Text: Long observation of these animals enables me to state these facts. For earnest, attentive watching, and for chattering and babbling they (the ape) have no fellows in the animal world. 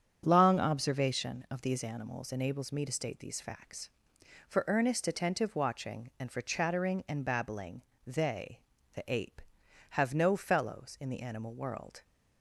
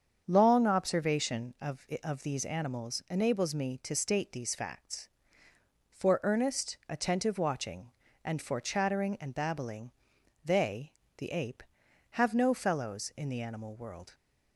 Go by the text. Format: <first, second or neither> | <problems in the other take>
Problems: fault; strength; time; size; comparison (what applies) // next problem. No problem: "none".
first | starts louder than the rest; strong; until 1.2 s; 7.5 dB; strong in the first // says "of" twice; at 2.0 s // pauses between "babbling" and "they"; noticeable; at 9.9 s; 0.50 s long; slight in the first